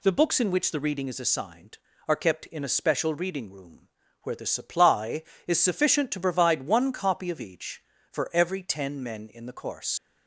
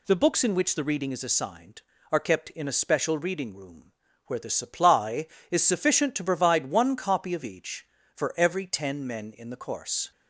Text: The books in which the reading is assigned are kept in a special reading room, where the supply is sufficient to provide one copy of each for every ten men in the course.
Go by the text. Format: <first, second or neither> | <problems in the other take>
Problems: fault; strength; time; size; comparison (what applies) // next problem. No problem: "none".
second | leaves "course" unfinished; at 9.9 s; 95 ms